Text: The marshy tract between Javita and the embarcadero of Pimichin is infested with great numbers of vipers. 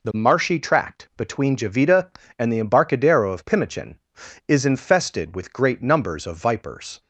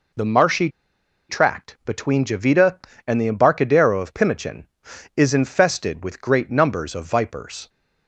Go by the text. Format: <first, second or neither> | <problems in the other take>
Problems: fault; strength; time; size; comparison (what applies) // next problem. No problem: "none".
first | pauses between "marshy" and "tract"; noticeable; at 0.6 s; 0.60 s long